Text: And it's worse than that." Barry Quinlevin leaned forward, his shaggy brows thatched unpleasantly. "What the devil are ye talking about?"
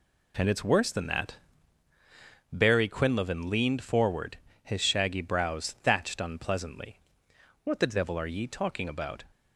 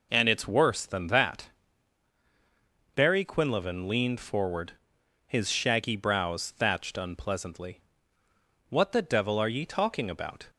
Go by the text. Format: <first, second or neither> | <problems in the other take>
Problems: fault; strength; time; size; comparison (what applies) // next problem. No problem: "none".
neither | none